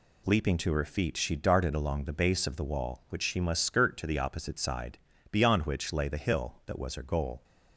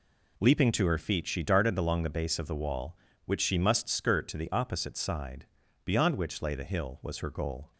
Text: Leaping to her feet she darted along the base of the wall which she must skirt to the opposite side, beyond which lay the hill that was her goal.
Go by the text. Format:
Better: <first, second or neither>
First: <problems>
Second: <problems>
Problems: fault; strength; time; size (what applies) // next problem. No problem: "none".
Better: first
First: none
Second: skips "that"; at 7.0 s